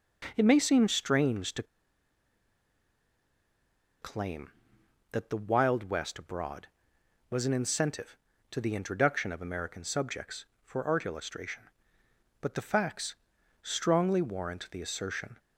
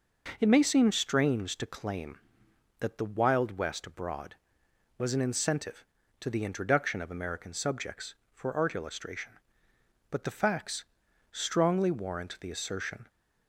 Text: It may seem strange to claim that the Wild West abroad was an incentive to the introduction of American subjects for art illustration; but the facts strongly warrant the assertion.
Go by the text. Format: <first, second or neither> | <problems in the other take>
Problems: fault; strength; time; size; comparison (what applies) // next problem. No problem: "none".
second | pauses between "to" and "claim"; strong; at 1.6 s; 2.3 s long // pauses between "facts" and "strongly"; noticeable; at 13.1 s; 0.48 s long; noticeable in the second